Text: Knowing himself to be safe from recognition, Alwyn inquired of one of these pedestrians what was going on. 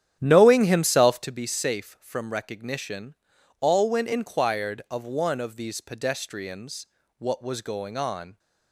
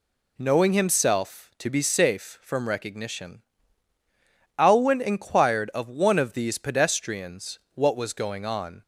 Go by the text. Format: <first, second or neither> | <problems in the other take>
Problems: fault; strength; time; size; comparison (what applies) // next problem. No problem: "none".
second | starts louder than the rest; strong; until 1.3 s; 10.5 dB // pauses between "pedestrians" and "what"; slight; at 6.8 s; 0.32 s long; slight in the second